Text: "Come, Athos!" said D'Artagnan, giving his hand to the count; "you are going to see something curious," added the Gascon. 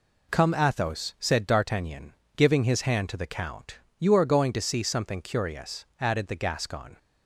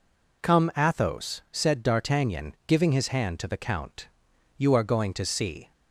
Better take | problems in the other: first | stops before "something curious added the Gascon"; at 5.7 s

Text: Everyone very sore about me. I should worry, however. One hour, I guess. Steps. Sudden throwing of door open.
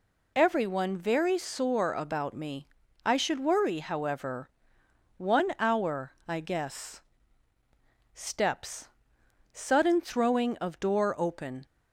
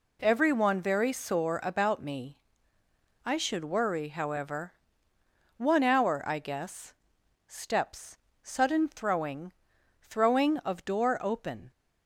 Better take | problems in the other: first | says "throwing" twice; at 10.0 s

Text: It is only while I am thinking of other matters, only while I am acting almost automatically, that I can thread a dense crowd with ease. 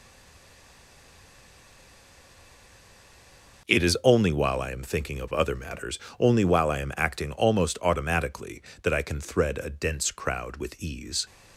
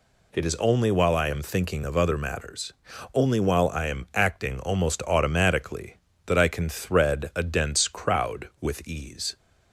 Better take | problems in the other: second | stays silent before the first word; strong; until 3.6 s; 3.6 s long

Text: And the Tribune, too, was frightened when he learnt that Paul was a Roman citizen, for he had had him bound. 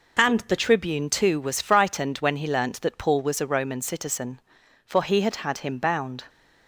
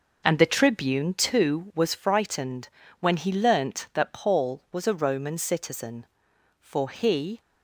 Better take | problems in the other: first | pauses between "frightened" and "when"; slight; at 2.6 s; 0.32 s long // stops before "had had him bound"; at 7.4 s

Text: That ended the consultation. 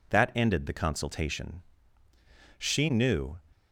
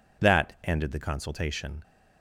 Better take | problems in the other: second | goes on to say "She knew"; noticeable; from 2.5 s on; 0.80 s long

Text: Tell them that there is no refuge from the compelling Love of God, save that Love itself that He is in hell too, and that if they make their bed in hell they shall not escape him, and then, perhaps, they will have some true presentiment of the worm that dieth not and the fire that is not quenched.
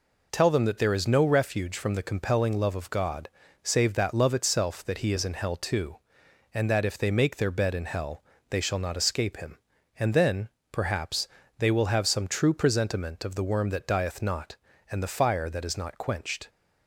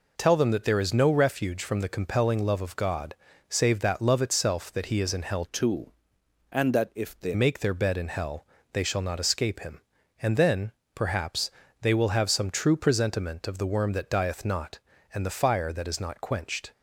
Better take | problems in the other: first | changes voice from "too" to "they"; from 5.4 to 7.3 s; 1.9 s long // pauses between "hell" and "they"; slight; at 8.4 s; 0.26 s long; slight in the first

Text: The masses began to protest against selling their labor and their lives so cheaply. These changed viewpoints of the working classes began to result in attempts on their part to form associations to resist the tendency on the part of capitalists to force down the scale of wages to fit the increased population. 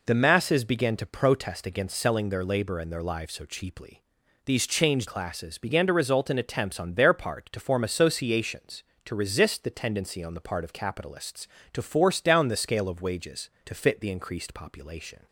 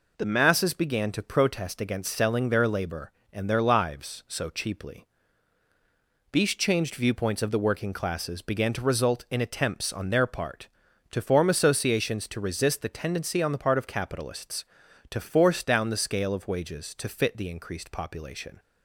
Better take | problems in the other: second | skips "viewpoints of the working"; at 5.0 s

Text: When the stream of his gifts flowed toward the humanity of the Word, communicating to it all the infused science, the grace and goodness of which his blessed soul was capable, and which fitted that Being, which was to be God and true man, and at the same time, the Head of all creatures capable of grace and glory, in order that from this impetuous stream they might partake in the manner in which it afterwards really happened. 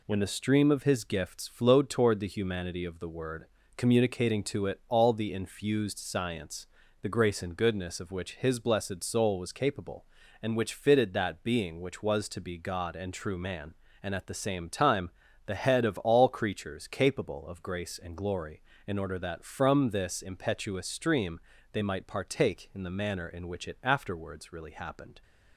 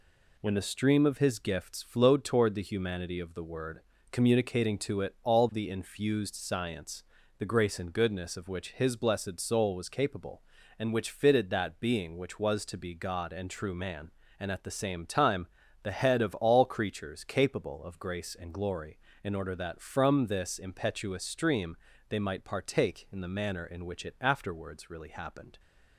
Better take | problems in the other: neither | pauses between "stream" and "they"; slight; the same in both

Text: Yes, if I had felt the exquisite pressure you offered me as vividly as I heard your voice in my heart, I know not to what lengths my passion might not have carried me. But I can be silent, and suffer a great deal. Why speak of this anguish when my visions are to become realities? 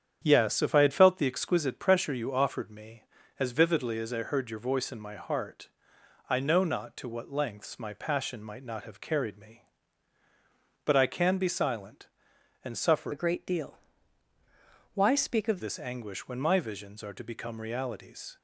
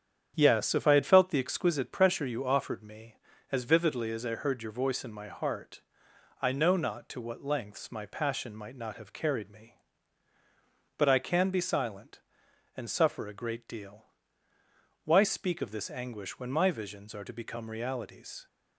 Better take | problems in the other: second | starts louder than the rest; strong; until 1.2 s; 8.5 dB; strong in the second // changes voice from "a" to "of"; from 13.1 to 15.6 s; 2.5 s long

